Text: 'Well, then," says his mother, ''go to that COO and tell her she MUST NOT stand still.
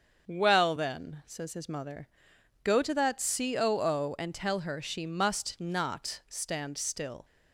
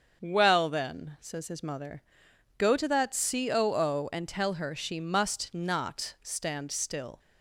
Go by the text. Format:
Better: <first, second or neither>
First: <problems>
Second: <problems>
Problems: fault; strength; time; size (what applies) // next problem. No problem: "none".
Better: neither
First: starts louder than the rest; until 1.3 s; 6.5 dB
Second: starts louder than the rest; until 1.2 s; 6.5 dB